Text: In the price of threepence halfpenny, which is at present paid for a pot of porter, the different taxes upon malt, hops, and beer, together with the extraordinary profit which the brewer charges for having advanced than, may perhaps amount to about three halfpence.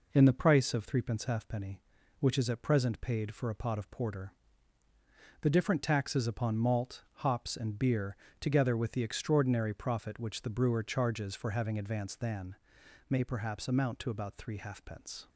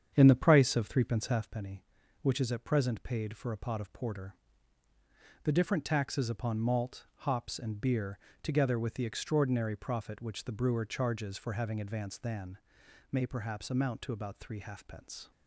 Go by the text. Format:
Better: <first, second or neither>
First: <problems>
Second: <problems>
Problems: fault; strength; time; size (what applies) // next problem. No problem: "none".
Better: first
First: none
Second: starts louder than the rest; strong; until 1.5 s; 8 dB